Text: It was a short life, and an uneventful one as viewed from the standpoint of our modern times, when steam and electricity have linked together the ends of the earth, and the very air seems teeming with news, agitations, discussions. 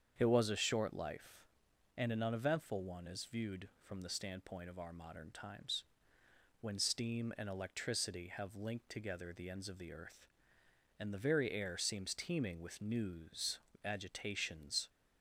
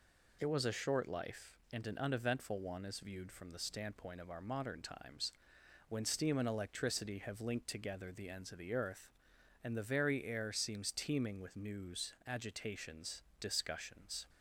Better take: second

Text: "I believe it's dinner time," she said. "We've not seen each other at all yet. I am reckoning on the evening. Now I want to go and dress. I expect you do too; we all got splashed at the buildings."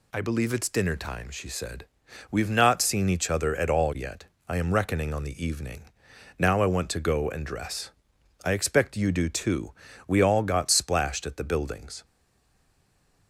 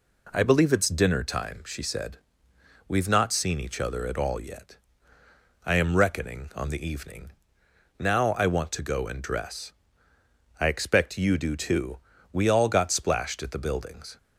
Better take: second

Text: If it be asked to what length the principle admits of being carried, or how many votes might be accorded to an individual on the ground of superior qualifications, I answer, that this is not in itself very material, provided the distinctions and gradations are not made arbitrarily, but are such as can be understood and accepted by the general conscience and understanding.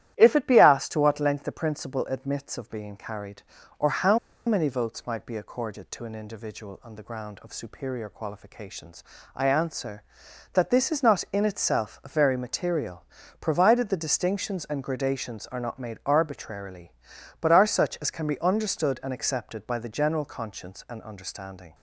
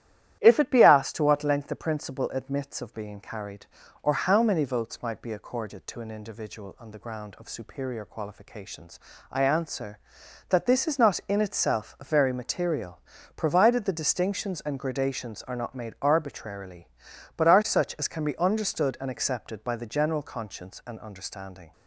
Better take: second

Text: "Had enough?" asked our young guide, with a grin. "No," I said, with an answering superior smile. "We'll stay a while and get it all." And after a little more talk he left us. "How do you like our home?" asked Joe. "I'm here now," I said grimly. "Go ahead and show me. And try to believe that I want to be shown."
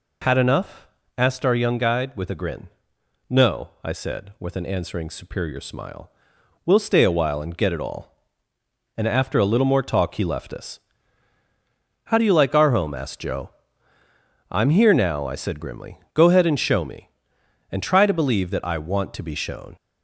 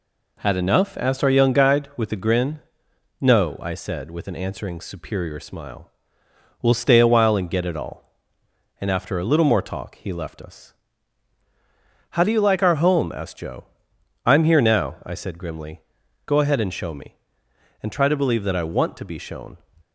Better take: neither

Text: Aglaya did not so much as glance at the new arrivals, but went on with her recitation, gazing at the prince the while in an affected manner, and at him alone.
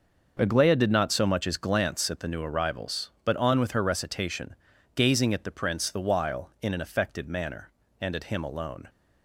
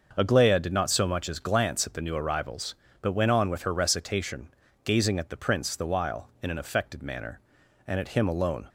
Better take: second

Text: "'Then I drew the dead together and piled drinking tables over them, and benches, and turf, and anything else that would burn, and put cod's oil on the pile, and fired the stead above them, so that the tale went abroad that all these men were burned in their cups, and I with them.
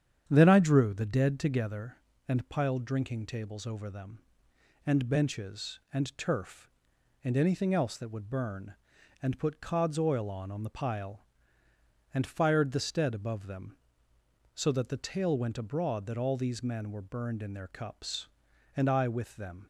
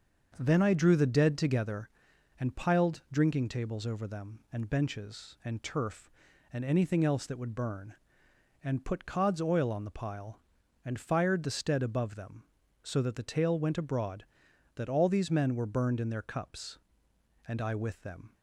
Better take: second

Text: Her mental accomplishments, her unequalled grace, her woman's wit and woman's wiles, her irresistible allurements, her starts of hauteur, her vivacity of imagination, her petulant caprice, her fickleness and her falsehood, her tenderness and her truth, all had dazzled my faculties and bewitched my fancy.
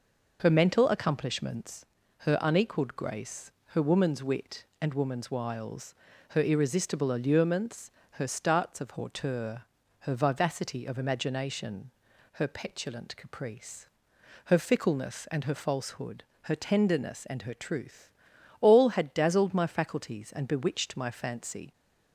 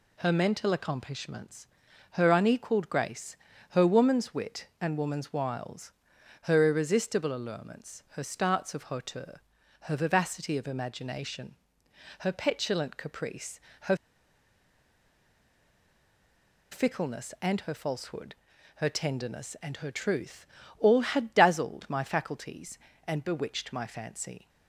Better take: first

